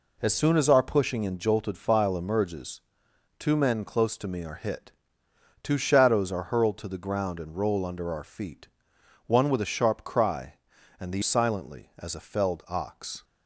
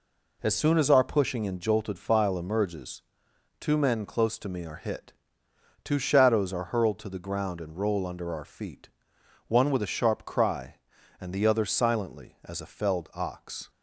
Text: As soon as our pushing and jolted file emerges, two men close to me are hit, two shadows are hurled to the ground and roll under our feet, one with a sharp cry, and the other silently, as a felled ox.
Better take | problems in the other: second | skips "other"; at 11.2 s

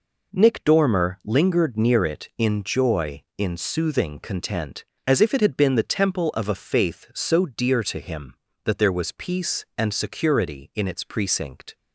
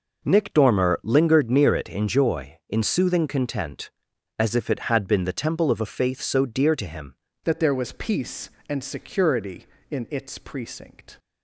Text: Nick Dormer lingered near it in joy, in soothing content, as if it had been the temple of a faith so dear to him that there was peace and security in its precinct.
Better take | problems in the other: first | changes voice at "that"; from 7.4 s on; 3.7 s long

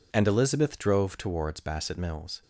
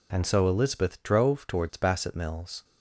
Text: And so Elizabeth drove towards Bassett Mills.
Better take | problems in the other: second | skips "so"; at 0.2 s

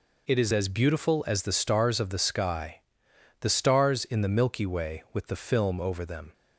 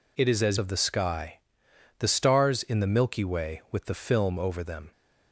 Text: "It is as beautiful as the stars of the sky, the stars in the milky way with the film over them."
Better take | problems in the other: first | skips "beautiful as the stars"; at 0.5 s

